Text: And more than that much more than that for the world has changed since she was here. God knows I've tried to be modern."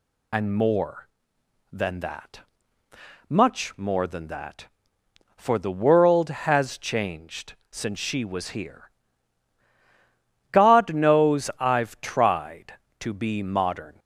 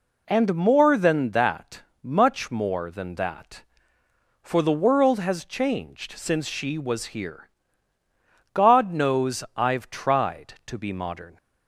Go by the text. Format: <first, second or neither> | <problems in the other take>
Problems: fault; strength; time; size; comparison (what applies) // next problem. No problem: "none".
second | loses the start of "And"; at 0.3 s; 40 ms // pauses between "that" and "much"; noticeable; at 2.4 s; 0.88 s long; slight in the second // pauses between "changed" and "since"; slight; at 7.5 s; 0.18 s long